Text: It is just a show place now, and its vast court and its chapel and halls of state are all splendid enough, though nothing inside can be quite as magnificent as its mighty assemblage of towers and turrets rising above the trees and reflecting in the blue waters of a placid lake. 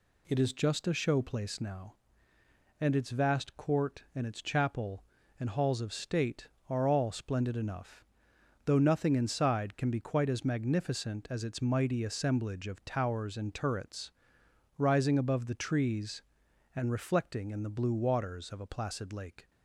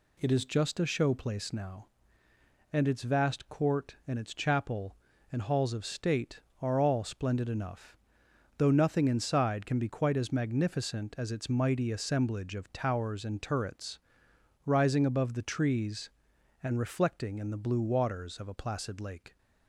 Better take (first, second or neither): neither